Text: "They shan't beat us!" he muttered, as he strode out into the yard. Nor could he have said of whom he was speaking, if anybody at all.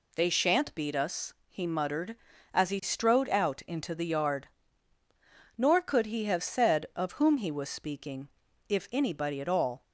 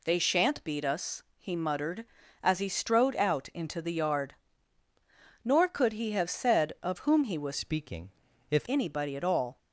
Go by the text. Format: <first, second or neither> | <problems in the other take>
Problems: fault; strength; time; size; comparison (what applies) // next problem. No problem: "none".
first | changes voice from "speaking" to "if"; from 7.5 to 8.6 s; 1.1 s long